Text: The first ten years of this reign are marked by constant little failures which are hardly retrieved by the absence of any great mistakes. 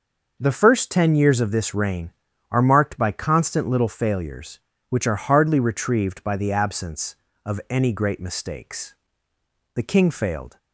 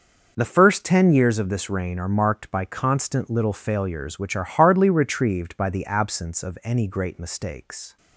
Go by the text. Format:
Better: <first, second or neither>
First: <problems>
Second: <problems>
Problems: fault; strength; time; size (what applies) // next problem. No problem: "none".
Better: second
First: goes on to say "The king failed"; noticeable; from 9.7 s on; 0.82 s long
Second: none